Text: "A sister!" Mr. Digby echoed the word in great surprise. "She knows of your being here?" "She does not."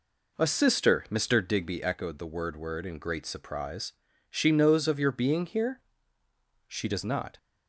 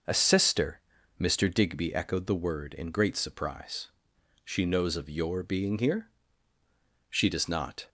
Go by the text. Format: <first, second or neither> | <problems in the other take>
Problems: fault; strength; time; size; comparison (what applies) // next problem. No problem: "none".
second | says "word" twice; at 2.5 s